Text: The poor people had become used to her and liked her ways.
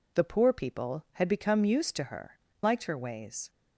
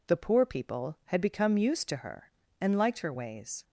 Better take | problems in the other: second | skips "and"; at 2.5 s

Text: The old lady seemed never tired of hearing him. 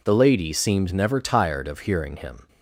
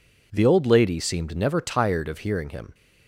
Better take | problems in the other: second | skips "old"; at 0.1 s

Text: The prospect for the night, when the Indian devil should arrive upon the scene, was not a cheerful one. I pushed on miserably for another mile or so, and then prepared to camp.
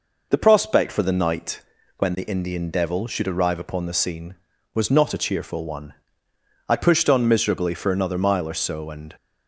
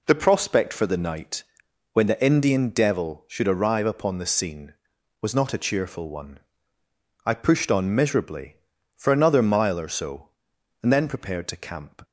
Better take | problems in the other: second | stops before "then prepared to camp"; at 9.1 s

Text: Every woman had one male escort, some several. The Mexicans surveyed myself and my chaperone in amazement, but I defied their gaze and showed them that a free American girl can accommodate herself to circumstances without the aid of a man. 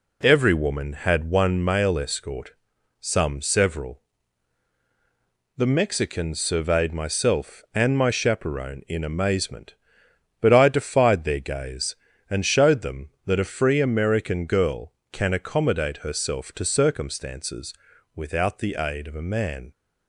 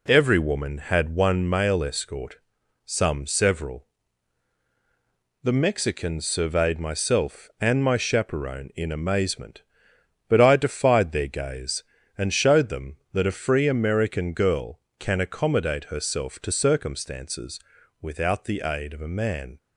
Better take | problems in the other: neither | pauses between "circumstances" and "without"; the same in both

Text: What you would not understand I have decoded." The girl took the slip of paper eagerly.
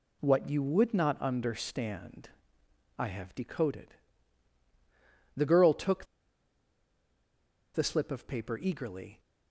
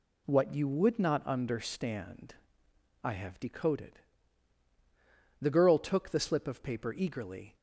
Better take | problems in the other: second | pauses between "understand" and "I"; noticeable; at 2.2 s; 0.68 s long; noticeable in the second // pauses between "took" and "the"; strong; at 6.0 s; 1.6 s long

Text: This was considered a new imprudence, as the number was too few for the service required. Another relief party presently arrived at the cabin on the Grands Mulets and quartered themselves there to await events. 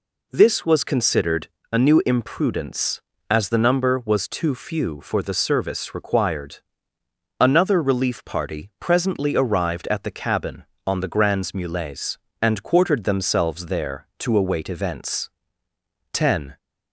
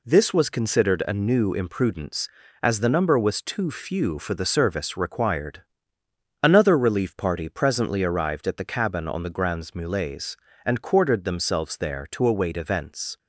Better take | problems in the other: second | pauses between "considered" and "a"; slight; at 1.4 s; 0.24 s long // goes on to say "Ten"; slight; from 16.1 s on; 0.44 s long

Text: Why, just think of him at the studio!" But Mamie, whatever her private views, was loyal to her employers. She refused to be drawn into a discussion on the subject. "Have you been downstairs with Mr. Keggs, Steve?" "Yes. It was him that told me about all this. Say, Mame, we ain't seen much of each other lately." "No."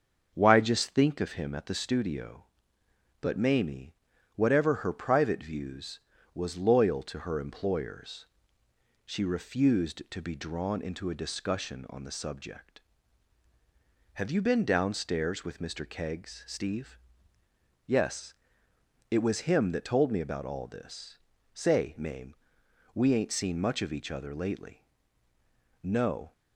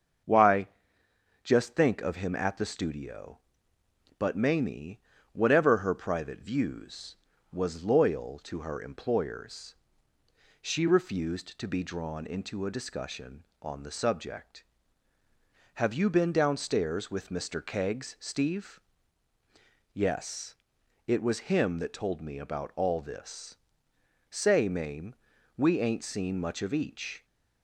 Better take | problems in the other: first | starts louder than the rest; until 2.0 s; 6.5 dB; also in the first // stops before "other lately No"; at 27.2 s

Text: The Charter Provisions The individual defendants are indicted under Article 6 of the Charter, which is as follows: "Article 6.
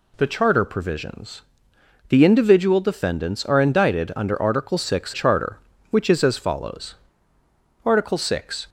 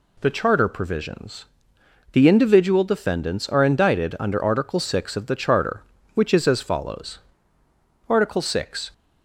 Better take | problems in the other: second | pauses between "Provisions" and "The"; noticeable; at 1.4 s; 0.66 s long; noticeable in the second // skips "of the"; at 5.1 s

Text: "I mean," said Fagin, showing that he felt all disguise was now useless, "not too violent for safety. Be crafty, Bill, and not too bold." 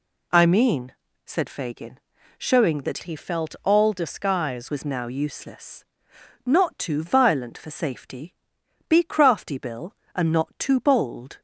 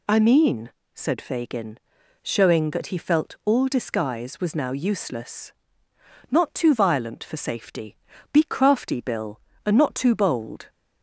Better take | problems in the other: second | changes voice from "he" to "disguise"; from 3.0 to 4.6 s; 1.6 s long

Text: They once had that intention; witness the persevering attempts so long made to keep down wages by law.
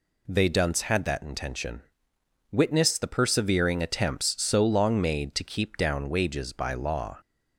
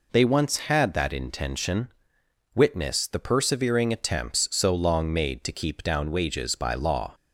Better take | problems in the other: second | says "dunce" for "once"; at 0.4 s

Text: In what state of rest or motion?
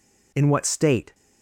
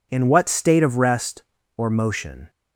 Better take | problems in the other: second | stops before "of rest or motion"; at 1.1 s

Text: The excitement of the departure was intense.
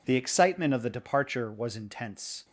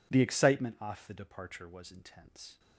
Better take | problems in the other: first | says "off" for "of"; at 0.7 s

